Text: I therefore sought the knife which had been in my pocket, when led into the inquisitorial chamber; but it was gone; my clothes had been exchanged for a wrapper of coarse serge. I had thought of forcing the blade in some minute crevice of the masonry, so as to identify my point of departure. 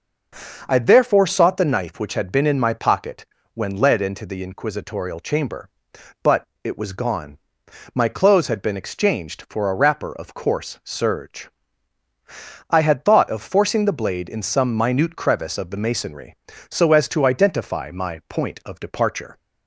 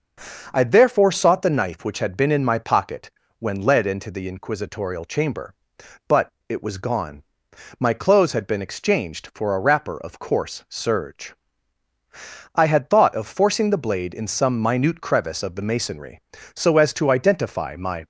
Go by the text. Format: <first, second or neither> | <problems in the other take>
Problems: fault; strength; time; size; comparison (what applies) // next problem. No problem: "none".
first | starts louder than the rest; until 1.5 s; 6 dB; also in the first // pauses between "but" and "it"; slight; at 6.3 s; 0.16 s long; slight in the first // stops before "point of departure"; at 18.0 s